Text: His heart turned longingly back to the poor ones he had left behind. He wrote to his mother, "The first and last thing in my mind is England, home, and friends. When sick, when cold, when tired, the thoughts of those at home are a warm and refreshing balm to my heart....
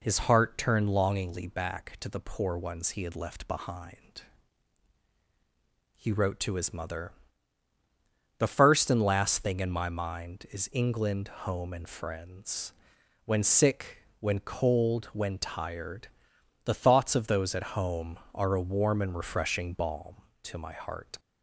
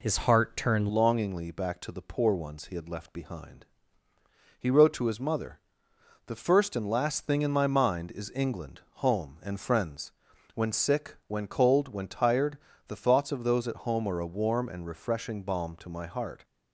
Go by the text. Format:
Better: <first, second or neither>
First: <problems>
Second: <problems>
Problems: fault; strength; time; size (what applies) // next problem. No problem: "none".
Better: first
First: none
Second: changes voice at "longingly"; from 0.9 s on; 15.5 s long